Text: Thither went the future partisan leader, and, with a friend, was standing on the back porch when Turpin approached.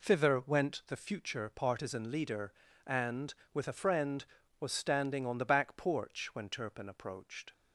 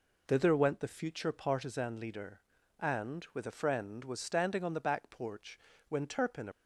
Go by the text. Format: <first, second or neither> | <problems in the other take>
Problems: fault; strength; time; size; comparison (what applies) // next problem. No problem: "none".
first | pauses between "porch" and "when"; slight; at 5.5 s; 0.30 s long // stops before "approached"; at 6.5 s